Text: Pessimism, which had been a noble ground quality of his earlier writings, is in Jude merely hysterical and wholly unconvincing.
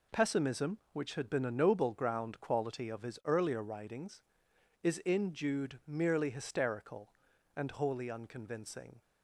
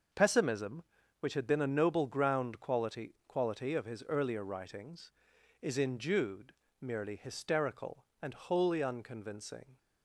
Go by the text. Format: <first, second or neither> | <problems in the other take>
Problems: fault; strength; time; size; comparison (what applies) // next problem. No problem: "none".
first | says "quality" twice; at 3.2 s // pauses between "Jude" and "merely"; slight; at 6.5 s; 0.30 s long